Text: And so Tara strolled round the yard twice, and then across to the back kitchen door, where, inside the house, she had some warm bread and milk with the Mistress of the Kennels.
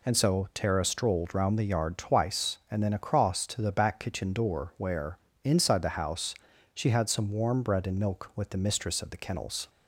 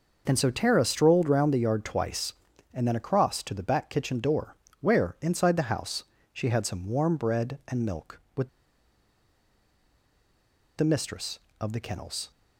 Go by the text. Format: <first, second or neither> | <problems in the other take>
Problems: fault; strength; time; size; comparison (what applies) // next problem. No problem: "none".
first | pauses between "with" and "the"; strong; at 8.4 s; 2.2 s long